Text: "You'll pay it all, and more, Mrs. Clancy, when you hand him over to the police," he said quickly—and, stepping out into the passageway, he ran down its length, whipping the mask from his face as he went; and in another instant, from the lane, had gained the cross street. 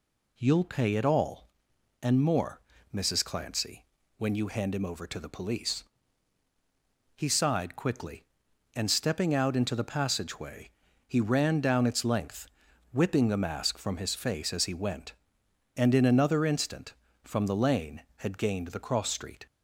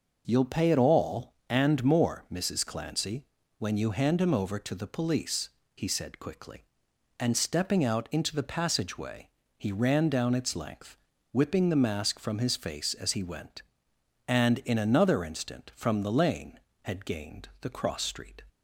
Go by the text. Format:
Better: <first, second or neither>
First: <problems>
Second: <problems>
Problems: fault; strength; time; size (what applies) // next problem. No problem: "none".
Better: second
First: says "sighed" for "said"; at 7.2 s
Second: none